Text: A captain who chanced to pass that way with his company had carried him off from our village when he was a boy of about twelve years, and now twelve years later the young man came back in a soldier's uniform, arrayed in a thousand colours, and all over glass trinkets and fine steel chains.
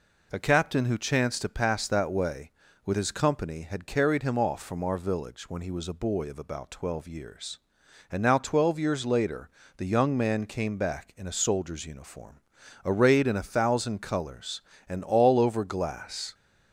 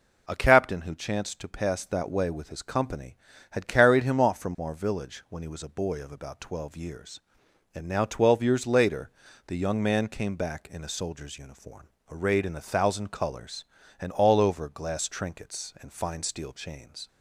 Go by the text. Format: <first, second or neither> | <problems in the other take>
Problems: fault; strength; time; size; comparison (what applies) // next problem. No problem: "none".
second | pauses between "later" and "the"; slight; at 9.4 s; 0.30 s long; slight in the second // stops before "trinkets and fine steel chains"; at 16.3 s